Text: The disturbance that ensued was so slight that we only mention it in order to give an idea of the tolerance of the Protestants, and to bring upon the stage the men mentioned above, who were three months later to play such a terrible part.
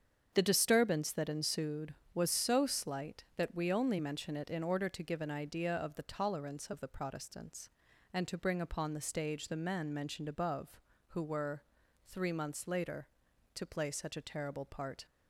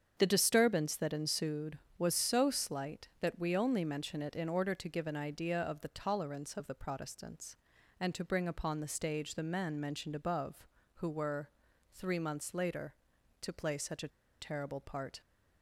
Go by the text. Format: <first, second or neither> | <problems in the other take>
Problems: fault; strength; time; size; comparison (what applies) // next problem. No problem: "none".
first | starts louder than the rest; strong; until 1.1 s; 7.5 dB; strong in the first // pauses between "were" and "three"; at 11.4 s; 0.42 s long; also in the first // pauses between "a" and "terrible"; slight; at 14.0 s; 0.31 s long